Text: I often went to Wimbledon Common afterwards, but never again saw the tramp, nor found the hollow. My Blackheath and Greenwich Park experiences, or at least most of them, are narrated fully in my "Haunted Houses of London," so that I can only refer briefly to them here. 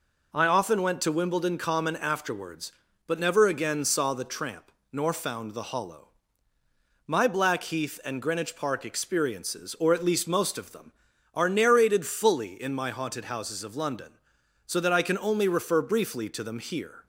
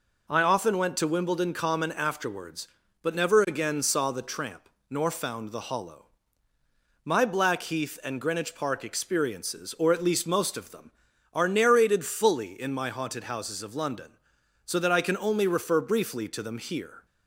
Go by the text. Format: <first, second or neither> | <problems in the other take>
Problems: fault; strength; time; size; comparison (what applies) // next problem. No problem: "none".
neither | none